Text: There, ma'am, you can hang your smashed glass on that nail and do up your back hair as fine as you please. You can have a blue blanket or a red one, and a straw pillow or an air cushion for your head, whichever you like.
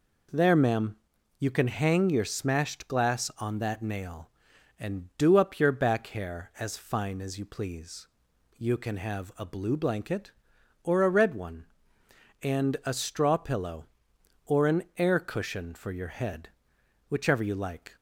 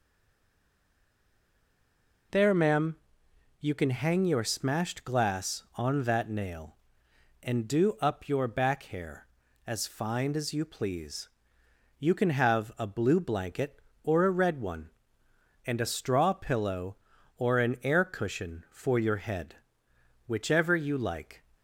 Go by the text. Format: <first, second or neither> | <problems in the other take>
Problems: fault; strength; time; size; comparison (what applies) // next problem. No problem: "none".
first | stays silent before the first word; until 2.3 s; 2.3 s long